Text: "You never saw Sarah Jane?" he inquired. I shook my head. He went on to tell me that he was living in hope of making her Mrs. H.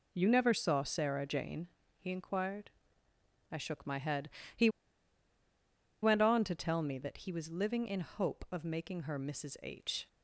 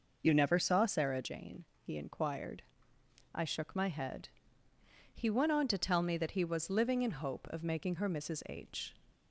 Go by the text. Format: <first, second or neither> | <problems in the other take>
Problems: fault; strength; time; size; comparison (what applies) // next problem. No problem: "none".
second | pauses between "He" and "went"; strong; at 4.6 s; 1.3 s long